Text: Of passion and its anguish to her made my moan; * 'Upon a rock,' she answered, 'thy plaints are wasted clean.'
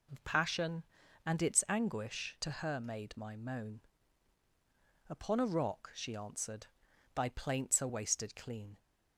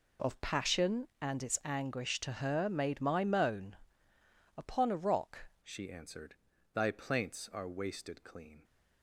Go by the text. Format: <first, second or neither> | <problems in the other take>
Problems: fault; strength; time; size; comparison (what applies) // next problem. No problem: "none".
first | changes voice at "she"; from 5.6 s on; 3.0 s long